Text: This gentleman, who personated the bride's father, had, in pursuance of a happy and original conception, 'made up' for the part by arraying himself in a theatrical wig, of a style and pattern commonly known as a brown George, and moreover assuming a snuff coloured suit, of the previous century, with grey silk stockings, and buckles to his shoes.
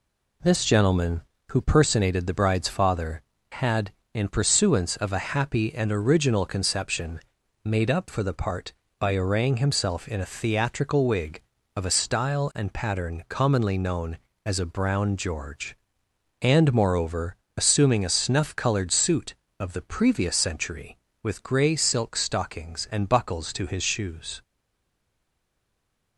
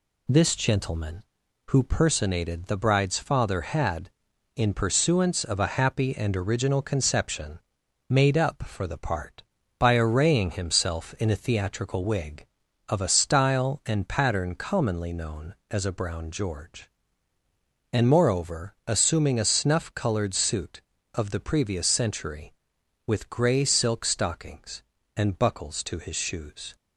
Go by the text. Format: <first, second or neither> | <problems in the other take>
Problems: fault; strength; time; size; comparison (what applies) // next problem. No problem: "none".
second | pauses between "moreover" and "assuming"; slight; at 17.3 s; 0.20 s long // stays silent after the last word; noticeable; from 24.4 s on; 1.7 s long